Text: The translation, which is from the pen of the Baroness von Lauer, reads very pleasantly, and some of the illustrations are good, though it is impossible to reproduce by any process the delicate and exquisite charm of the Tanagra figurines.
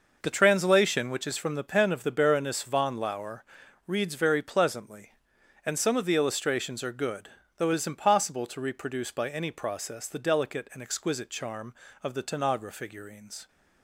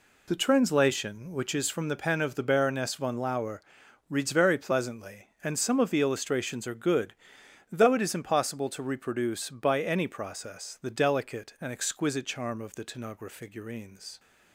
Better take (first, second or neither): neither